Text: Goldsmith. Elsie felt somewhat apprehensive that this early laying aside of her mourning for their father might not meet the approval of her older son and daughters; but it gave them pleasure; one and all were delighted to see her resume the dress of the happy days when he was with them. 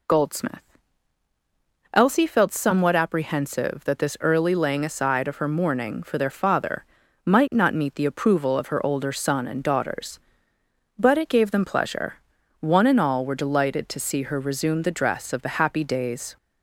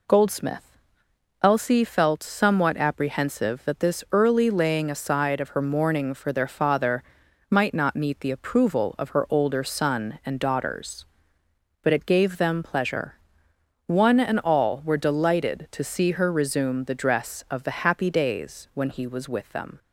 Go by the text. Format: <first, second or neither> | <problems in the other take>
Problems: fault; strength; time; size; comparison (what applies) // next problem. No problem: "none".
second | pauses between "father" and "might"; at 6.8 s; 0.40 s long; noticeable in the second // stops before "when he was with them"; at 16.3 s